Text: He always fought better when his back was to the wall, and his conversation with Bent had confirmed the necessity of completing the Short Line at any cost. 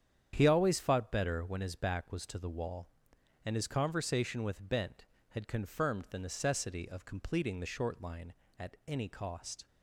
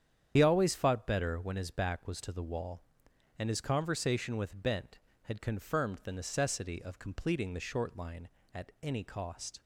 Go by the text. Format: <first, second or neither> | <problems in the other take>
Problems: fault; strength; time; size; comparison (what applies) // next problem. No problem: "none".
first | loses the start of "He"; at 0.3 s; 65 ms // starts louder than the rest; strong; until 1.3 s; 9 dB; strong in the first